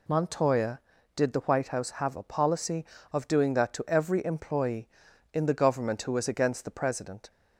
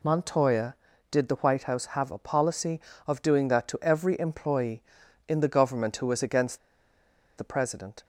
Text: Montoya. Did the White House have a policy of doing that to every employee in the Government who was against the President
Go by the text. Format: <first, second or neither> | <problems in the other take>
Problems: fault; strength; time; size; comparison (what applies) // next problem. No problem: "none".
first | pauses between "against" and "the"; noticeable; at 6.5 s; 0.79 s long